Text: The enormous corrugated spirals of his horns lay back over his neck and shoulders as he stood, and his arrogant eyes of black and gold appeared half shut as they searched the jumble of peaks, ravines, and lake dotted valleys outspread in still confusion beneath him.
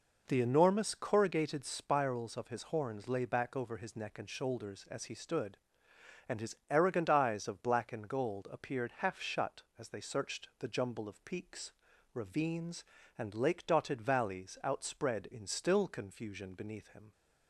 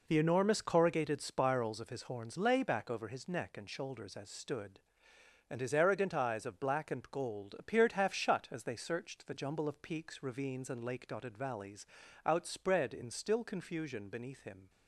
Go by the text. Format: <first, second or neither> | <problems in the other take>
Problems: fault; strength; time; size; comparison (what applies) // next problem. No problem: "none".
first | skips "he"; at 4.2 s // pauses between "valleys" and "outspread"; slight; at 11.8 s; 0.36 s long